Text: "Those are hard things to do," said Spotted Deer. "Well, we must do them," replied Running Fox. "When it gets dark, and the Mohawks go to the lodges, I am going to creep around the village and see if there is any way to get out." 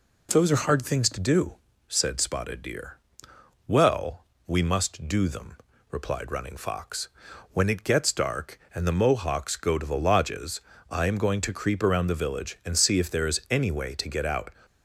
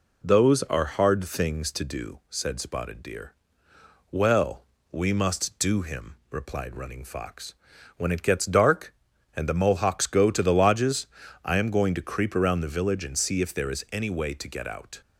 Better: first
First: none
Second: says "him" for "them"; at 5.8 s

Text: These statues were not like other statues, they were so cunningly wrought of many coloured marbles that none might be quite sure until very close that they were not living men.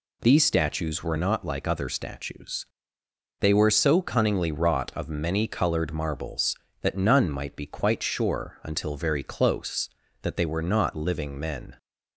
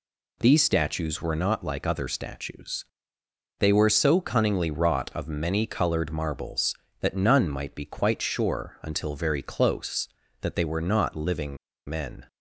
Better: first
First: none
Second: pauses between "living" and "men"; slight; at 11.5 s; 0.30 s long

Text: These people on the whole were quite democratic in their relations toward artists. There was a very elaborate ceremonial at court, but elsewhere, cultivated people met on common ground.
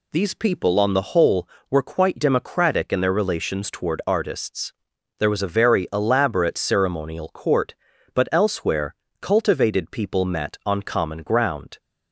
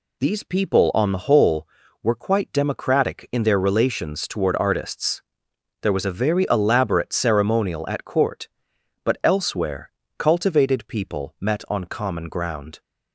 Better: second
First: skips "at"; at 7.2 s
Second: none

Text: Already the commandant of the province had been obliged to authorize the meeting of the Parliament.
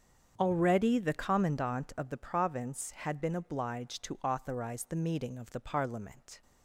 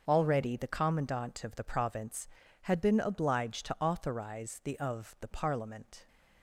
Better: first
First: starts louder than the rest; strong; until 1.3 s; 7.5 dB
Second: starts louder than the rest; until 1.0 s; 6.5 dB // skips "meeting"; at 4.7 s

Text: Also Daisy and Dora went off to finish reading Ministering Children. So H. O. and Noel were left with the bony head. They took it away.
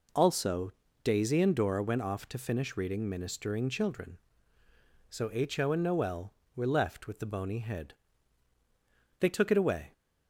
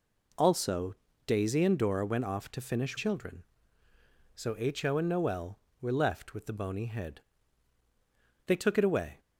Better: first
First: pauses between "Also" and "Daisy"; slight; at 0.7 s; 0.32 s long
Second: pauses between "Also" and "Daisy"; slight; at 0.9 s; 0.32 s long // skips "reading Ministering"; at 2.9 s

